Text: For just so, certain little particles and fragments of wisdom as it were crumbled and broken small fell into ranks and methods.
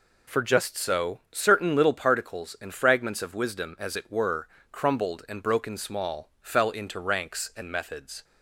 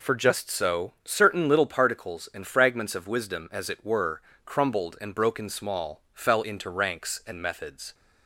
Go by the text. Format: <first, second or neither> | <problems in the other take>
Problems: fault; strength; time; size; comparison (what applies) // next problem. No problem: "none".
neither | pauses between "were" and "crumbled"; slight; the same in both